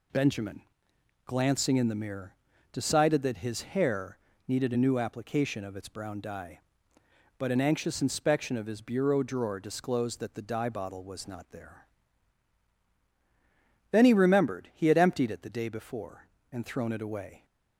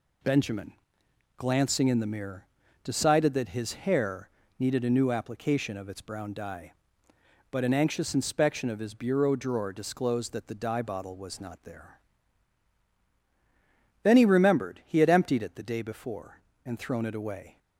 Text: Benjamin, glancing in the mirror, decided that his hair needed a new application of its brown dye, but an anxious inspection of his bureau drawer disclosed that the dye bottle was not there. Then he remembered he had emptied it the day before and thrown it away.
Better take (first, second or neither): neither